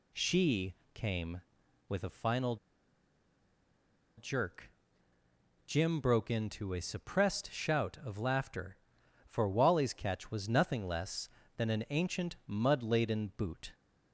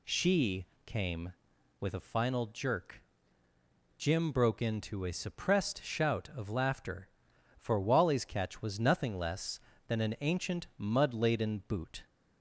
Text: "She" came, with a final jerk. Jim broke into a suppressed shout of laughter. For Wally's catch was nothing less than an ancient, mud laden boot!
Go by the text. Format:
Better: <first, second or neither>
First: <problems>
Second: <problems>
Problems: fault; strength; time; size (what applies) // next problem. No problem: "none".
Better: second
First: pauses between "She" and "came"; slight; at 0.7 s; 0.18 s long // pauses between "final" and "jerk"; strong; at 2.5 s; 1.6 s long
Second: pauses between "She" and "came"; slight; at 0.6 s; 0.18 s long